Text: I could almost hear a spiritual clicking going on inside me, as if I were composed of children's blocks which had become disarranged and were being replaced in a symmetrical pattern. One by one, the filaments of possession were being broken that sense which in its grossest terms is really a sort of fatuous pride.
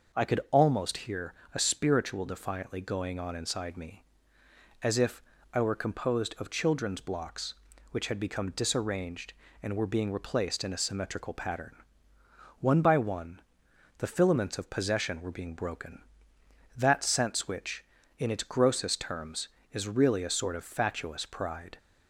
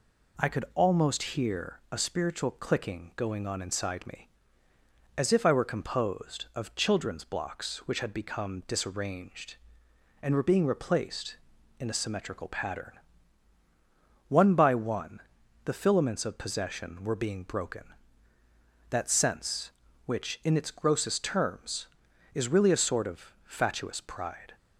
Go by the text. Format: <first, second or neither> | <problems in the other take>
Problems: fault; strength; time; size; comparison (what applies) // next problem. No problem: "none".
second | pauses between "hear" and "a"; slight; at 1.3 s; 0.22 s long // says "defiantly" for "clicking"; at 2.2 s // pauses between "if" and "I"; slight; at 5.2 s; 0.32 s long